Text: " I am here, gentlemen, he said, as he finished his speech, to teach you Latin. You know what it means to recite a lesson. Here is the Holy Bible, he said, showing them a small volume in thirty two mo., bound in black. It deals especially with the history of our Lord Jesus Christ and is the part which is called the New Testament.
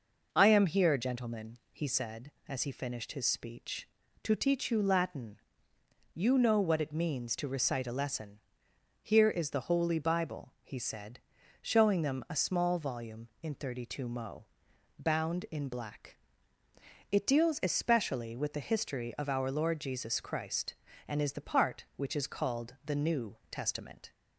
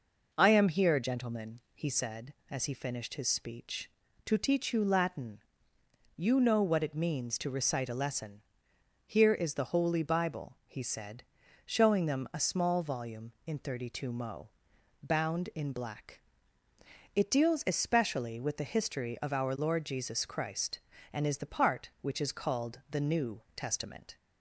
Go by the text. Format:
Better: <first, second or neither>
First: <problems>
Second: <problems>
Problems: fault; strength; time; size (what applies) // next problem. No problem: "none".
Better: neither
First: none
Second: none